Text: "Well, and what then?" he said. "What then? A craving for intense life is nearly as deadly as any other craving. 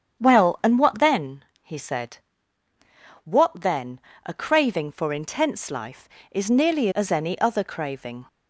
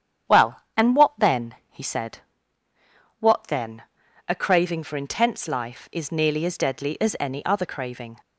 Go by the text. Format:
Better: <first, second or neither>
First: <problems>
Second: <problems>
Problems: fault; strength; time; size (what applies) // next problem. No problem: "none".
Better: second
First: starts louder than the rest; strong; until 1.2 s; 8 dB // skips "as deadly"; at 6.9 s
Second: starts louder than the rest; strong; until 1.4 s; 9 dB